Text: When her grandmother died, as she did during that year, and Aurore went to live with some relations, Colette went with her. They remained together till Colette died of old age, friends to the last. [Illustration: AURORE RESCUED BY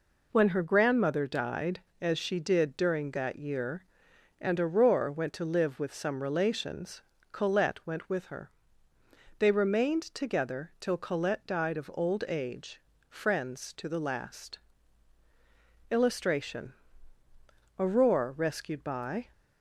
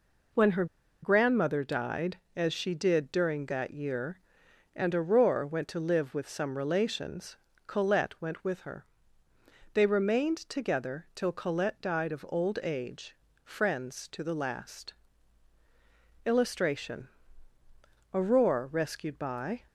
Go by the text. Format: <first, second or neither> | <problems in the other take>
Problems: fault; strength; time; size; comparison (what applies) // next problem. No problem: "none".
first | pauses between "her" and "grandmother"; at 0.6 s; 0.37 s long